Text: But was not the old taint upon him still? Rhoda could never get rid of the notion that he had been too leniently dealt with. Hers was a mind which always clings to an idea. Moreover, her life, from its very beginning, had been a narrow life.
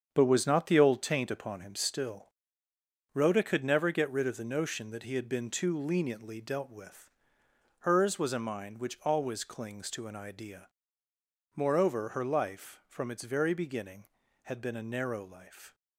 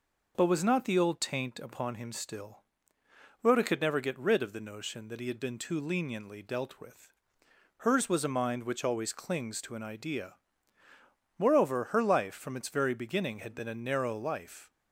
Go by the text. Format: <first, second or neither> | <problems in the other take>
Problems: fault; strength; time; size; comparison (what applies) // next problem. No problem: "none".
second | gets quieter; strong; throughout; 8.5 dB